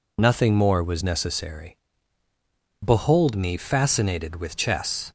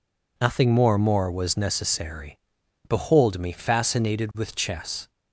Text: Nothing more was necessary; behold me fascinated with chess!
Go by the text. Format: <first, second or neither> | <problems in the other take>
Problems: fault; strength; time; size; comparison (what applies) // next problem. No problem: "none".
first | says "more" twice; at 0.9 s